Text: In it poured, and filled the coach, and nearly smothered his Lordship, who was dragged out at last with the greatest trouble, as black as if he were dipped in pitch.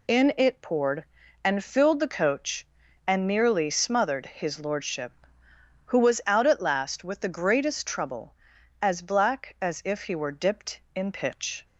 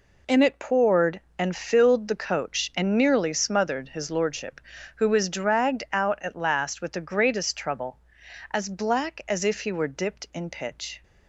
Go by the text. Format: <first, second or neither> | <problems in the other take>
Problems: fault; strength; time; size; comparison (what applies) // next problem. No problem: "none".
second | skips "dragged"; at 6.2 s